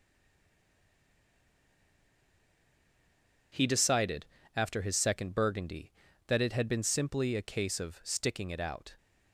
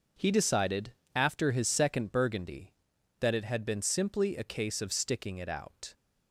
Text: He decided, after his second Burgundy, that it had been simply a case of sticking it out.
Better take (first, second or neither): second